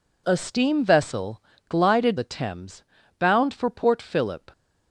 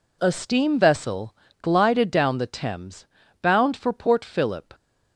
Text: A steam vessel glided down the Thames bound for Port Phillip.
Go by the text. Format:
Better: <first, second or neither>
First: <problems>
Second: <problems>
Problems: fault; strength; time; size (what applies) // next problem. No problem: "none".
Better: second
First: pauses between "vessel" and "glided"; slight; at 1.4 s; 0.26 s long // skips "down"; at 2.1 s // pauses between "Thames" and "bound"; at 2.8 s; 0.38 s long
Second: pauses between "vessel" and "glided"; slight; at 1.3 s; 0.26 s long // pauses between "Thames" and "bound"; at 3.0 s; 0.38 s long